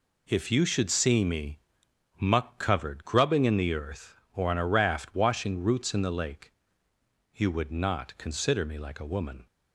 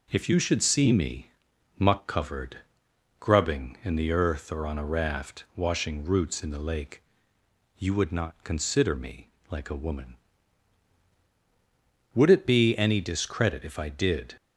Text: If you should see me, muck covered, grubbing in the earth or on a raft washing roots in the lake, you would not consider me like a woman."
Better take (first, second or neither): first